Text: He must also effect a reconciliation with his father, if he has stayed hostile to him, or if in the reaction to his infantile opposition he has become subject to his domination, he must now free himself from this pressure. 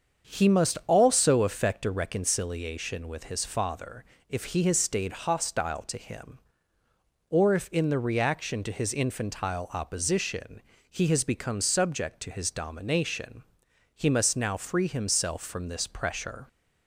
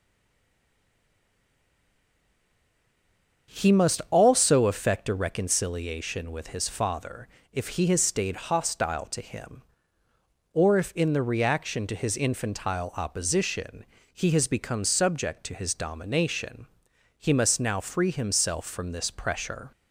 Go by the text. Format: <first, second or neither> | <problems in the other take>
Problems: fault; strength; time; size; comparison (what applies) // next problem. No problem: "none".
first | stays silent before the first word; strong; until 3.4 s; 3.4 s long // starts louder than the rest; until 4.5 s; 7 dB; also in the first // pauses between "opposition" and "he"; slight; at 13.8 s; 0.28 s long; slight in the first